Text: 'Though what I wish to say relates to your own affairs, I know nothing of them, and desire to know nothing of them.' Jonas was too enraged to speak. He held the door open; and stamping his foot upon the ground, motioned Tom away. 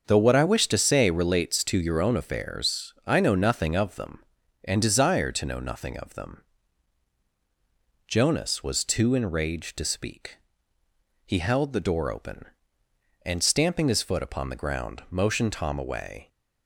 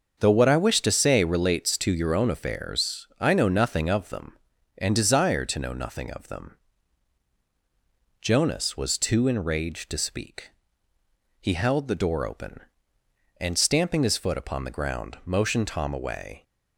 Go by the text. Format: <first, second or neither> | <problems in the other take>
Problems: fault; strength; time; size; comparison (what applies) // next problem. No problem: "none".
neither | starts louder than the rest; the same in both